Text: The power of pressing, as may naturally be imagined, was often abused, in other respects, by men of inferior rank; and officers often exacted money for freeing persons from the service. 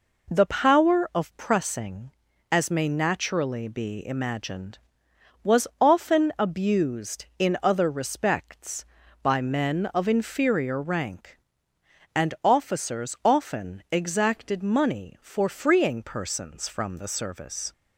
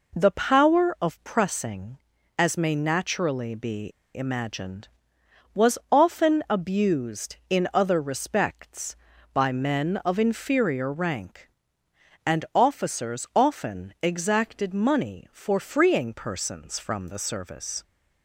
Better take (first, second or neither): first